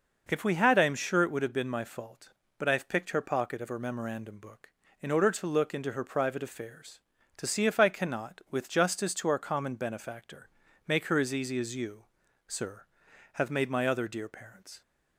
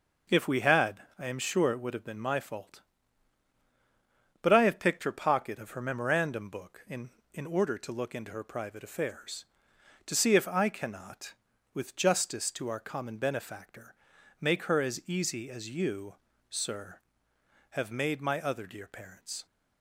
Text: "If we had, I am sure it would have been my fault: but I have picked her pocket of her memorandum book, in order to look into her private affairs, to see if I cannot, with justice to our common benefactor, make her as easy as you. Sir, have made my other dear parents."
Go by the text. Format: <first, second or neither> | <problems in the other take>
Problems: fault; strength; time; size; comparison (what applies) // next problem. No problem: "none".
first | says "in" twice; at 7.3 s